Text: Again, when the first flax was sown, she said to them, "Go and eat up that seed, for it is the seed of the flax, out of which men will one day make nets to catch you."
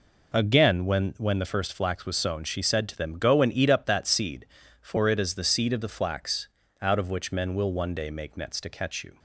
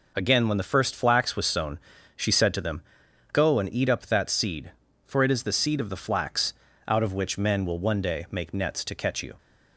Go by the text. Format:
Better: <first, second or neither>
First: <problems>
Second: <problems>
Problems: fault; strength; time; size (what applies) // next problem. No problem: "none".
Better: second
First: says "when" twice; at 1.1 s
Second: none